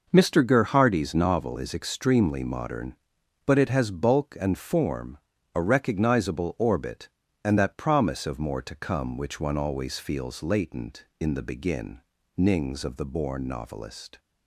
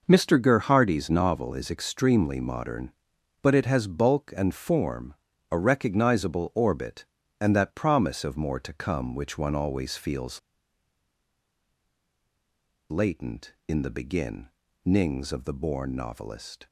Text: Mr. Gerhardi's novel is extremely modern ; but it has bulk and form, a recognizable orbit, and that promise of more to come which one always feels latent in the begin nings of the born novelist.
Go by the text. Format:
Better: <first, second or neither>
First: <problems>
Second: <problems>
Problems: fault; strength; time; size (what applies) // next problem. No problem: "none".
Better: first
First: pauses between "begin" and "nings"; slight; at 12.0 s; 0.36 s long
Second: pauses between "feels" and "latent"; strong; at 10.3 s; 2.5 s long // pauses between "begin" and "nings"; slight; at 14.4 s; 0.36 s long